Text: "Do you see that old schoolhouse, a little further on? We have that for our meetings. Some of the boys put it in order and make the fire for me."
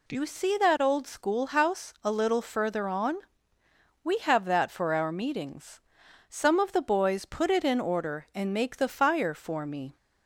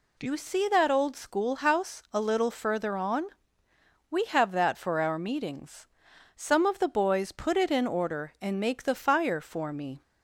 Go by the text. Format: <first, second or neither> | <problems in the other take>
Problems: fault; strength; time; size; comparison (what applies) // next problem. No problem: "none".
neither | none